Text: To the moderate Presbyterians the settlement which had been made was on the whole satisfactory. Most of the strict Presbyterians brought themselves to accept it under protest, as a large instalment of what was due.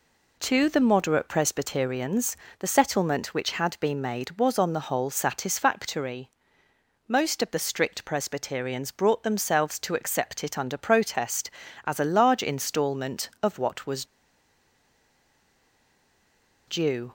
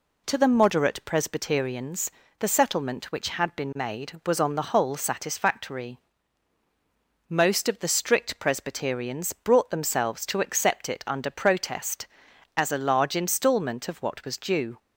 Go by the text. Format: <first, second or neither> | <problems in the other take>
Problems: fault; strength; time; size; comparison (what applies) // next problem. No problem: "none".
second | pauses between "Presbyterians" and "the"; slight; at 2.3 s; 0.24 s long; slight in the second // pauses between "was" and "due"; strong; at 14.0 s; 2.6 s long